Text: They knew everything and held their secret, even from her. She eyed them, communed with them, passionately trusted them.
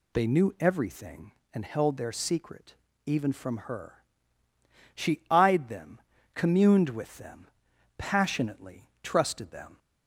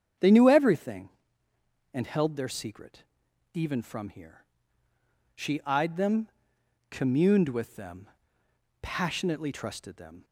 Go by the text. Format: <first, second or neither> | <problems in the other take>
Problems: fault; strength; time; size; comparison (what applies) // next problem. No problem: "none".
first | starts louder than the rest; strong; until 2.0 s; 8 dB // says "here" for "her"; at 4.1 s